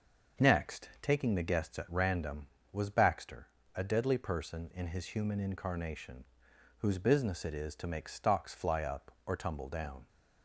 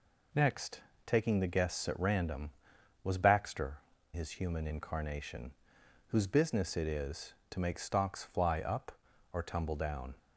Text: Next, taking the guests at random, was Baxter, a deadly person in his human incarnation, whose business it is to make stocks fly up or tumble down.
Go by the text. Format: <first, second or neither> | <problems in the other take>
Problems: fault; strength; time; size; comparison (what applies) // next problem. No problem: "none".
first | skips "a deadly person in"; at 3.9 s